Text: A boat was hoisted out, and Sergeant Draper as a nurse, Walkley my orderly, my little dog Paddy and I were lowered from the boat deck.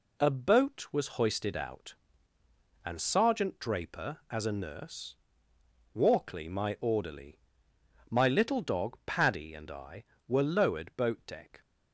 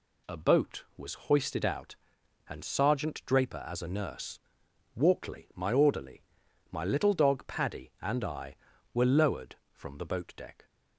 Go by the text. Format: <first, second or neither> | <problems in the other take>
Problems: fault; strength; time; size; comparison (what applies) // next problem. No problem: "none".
second | skips "from the"; at 10.9 s